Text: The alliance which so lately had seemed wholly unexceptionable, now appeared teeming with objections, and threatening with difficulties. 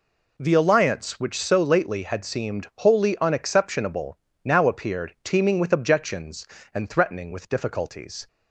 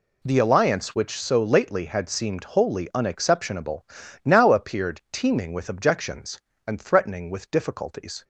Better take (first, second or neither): neither